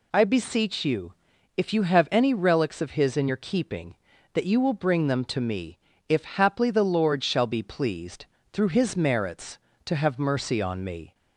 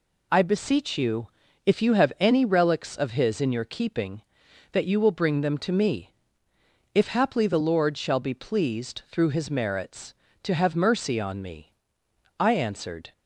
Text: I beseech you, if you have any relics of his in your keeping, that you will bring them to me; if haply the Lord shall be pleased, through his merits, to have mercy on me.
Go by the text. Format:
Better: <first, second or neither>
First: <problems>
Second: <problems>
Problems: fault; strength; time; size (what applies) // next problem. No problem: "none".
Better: first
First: none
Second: goes on to say "I answered"; noticeable; from 12.3 s on; 0.74 s long